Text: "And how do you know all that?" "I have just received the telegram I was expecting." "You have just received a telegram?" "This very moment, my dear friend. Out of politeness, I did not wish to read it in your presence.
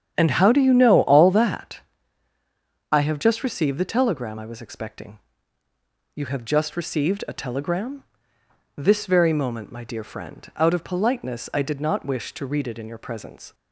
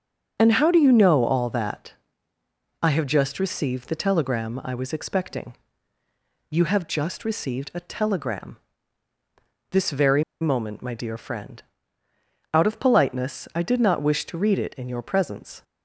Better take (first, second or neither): first